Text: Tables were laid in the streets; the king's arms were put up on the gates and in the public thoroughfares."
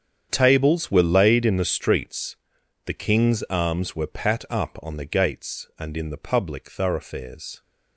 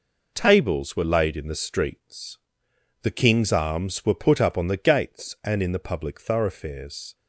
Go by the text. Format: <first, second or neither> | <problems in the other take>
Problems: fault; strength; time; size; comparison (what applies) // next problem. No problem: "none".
second | starts louder than the rest; strong; until 1.3 s; 8 dB // says "pat" for "put"; at 4.0 s